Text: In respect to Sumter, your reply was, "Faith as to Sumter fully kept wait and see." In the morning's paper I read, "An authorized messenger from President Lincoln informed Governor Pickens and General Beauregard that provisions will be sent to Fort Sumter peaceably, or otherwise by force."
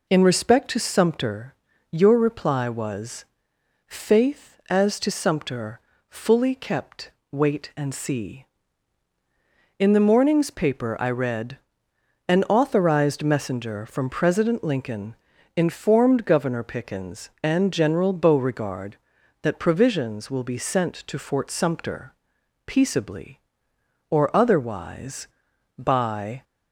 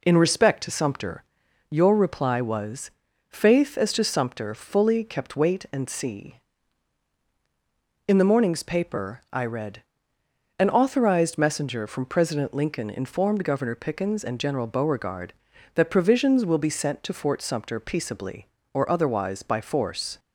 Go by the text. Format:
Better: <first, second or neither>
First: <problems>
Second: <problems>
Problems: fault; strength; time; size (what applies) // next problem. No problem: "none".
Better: second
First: pauses between "Sumter" and "fully"; slight; at 5.8 s; 0.28 s long // pauses between "kept" and "wait"; slight; at 7.1 s; 0.18 s long // pauses between "Lincoln" and "informed"; at 15.1 s; 0.42 s long // stops before "force"; at 26.4 s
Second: none